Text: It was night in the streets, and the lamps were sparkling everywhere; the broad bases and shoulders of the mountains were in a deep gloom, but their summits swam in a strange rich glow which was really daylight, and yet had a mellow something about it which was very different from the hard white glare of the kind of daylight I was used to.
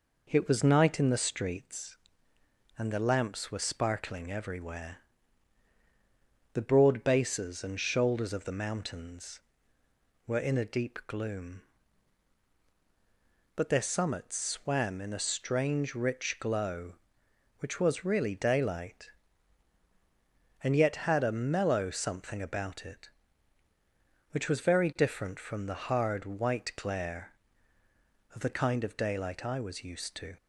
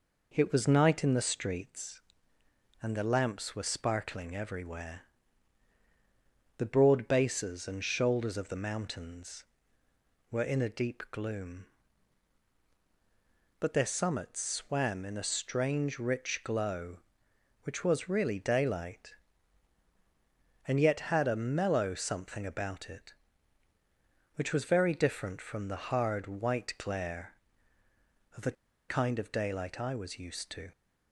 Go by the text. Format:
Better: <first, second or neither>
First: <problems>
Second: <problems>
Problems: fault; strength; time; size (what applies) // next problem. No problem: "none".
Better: first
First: none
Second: pauses between "the" and "kind"; at 28.5 s; 0.36 s long